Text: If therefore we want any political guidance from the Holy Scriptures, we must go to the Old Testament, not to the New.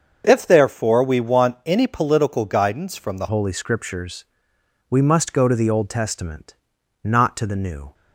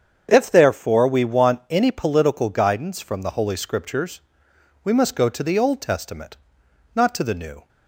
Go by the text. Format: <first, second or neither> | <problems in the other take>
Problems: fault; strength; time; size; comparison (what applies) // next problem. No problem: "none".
second | starts louder than the rest; until 1.2 s; 6.5 dB; strong in the second // changes voice at "Holy"; from 3.2 s on; 4.7 s long